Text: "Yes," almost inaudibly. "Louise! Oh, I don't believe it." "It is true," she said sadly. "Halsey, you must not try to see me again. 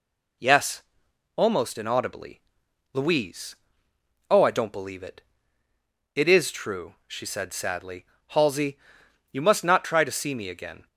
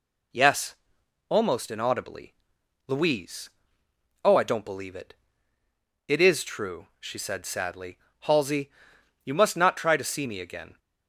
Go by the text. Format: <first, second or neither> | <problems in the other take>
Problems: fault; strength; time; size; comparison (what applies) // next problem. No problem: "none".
neither | none